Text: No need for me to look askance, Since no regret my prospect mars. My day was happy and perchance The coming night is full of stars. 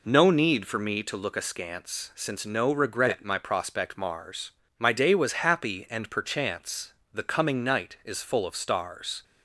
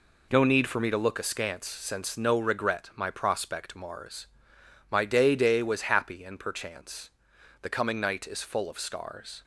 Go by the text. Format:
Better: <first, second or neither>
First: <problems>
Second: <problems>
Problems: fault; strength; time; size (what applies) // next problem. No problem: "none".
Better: first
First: pauses between "perchance" and "The"; slight; at 6.9 s; 0.18 s long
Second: says "day" twice; at 5.3 s // pauses between "perchance" and "The"; noticeable; at 7.0 s; 0.52 s long